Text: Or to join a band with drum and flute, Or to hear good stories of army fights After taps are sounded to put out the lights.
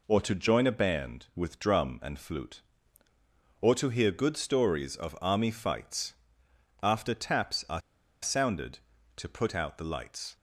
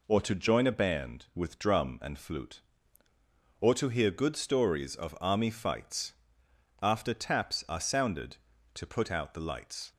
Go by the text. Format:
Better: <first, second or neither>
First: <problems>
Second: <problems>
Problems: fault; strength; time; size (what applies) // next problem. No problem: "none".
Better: second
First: pauses between "fights" and "After"; noticeable; at 6.1 s; 0.68 s long // pauses between "are" and "sounded"; at 7.8 s; 0.42 s long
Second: pauses between "fights" and "After"; noticeable; at 6.1 s; 0.68 s long